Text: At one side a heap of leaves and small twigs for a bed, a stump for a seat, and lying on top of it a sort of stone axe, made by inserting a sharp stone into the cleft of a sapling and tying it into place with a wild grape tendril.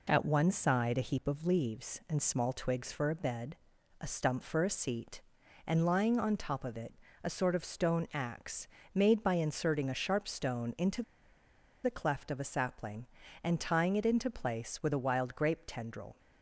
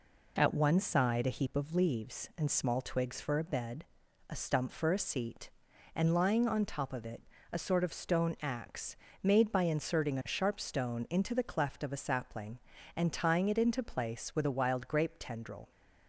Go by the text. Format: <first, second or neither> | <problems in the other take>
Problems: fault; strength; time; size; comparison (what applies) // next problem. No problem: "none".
second | pauses between "it" and "a"; slight; at 6.9 s; 0.28 s long; slight in the second // pauses between "into" and "the"; noticeable; at 11.0 s; 0.81 s long